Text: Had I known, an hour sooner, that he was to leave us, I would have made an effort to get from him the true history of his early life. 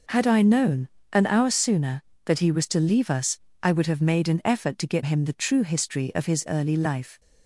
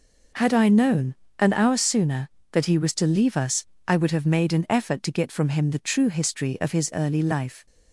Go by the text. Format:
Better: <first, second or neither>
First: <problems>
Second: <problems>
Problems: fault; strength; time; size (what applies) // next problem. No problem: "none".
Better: second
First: skips "from"; at 5.0 s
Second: none